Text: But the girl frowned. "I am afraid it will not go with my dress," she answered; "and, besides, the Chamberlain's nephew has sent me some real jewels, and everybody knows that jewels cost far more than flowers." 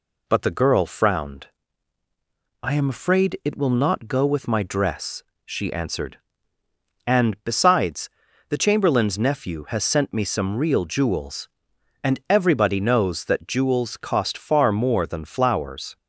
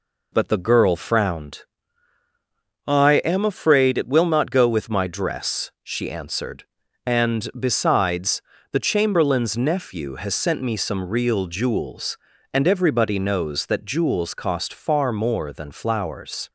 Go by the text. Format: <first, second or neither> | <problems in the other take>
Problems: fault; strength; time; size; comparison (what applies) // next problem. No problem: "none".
neither | none